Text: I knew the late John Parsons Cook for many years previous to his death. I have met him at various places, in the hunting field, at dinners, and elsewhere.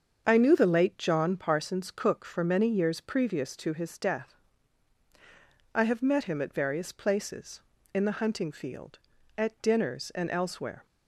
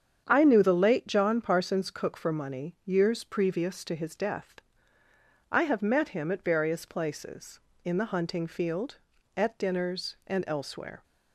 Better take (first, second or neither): first